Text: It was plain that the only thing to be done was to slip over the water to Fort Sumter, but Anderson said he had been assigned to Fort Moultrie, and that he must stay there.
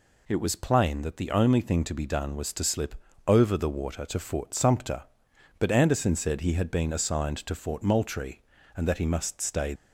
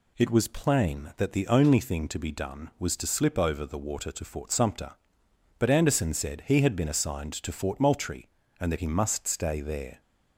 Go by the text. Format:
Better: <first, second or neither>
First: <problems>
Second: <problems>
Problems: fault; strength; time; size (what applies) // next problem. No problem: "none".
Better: second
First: pauses between "slip" and "over"; slight; at 2.9 s; 0.32 s long // stops before "there"; at 9.7 s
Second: none